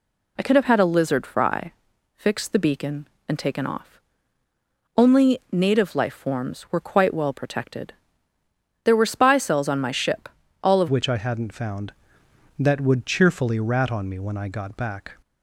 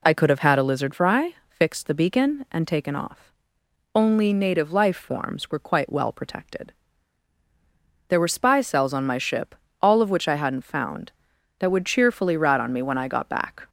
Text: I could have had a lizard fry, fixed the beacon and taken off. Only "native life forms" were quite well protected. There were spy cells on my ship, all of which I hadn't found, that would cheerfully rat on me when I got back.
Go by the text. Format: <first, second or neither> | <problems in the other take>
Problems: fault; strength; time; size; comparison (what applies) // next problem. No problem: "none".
second | changes voice at "which"; from 10.8 s on; 4.3 s long